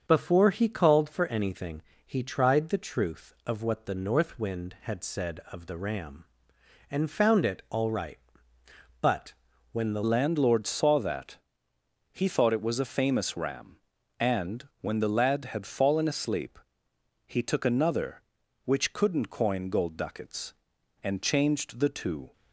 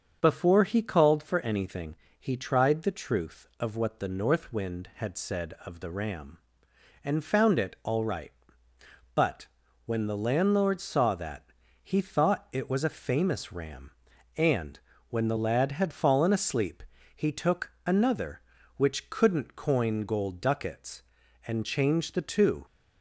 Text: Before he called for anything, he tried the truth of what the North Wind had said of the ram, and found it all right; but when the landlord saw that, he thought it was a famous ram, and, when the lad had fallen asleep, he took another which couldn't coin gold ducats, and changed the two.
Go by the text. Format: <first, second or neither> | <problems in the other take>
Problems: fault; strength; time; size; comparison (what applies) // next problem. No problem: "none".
second | starts louder than the rest; until 1.0 s; 6 dB; also in the second // pauses between "but" and "when"; at 9.3 s; 0.40 s long; also in the second // changes voice at "landlord"; from 10.0 s on; 12.3 s long